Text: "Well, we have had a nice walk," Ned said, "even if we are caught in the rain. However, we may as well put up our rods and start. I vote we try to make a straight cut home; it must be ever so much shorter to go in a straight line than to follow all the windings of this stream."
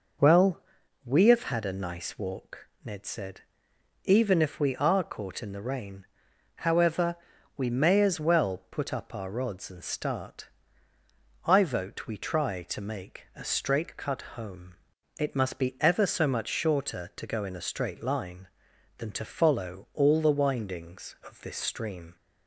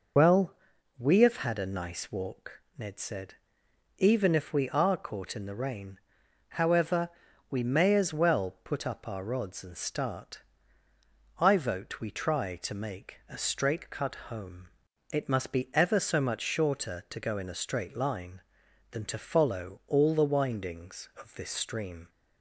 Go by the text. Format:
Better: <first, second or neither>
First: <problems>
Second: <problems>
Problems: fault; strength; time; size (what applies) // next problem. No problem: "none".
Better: first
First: none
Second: loses the start of "Well"; at 0.1 s; 30 ms